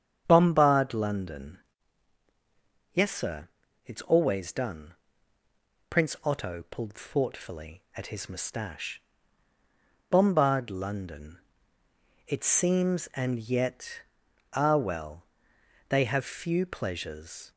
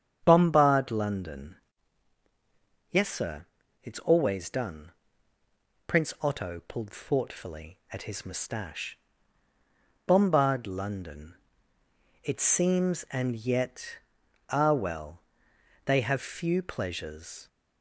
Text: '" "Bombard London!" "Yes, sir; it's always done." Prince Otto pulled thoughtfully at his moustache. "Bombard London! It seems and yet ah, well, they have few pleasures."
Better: neither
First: starts louder than the rest; strong; until 1.2 s; 8 dB // pauses between "yet" and "ah"; noticeable; at 14.0 s; 0.52 s long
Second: starts louder than the rest; strong; until 1.2 s; 8 dB // pauses between "yet" and "ah"; noticeable; at 13.9 s; 0.52 s long

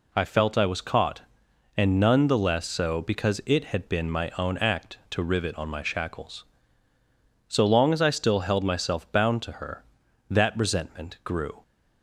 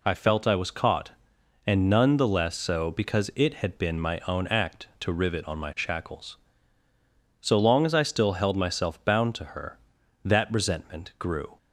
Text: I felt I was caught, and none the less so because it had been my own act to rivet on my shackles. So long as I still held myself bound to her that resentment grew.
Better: neither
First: none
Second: none

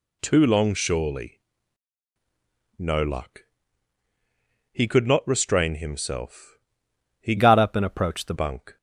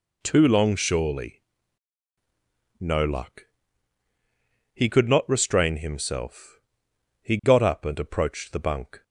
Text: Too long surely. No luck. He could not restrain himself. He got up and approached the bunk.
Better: second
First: changes voice from "got" to "the"; from 7.3 to 8.3 s; 1.0 s long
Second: none

